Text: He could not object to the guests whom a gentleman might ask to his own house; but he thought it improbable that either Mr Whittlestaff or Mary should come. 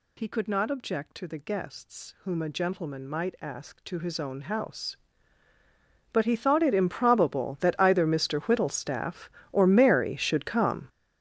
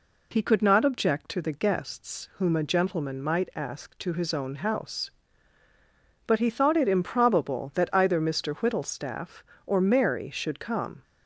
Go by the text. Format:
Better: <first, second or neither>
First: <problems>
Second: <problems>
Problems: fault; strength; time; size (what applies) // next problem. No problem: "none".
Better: second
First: gets louder; strong; throughout; 14 dB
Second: none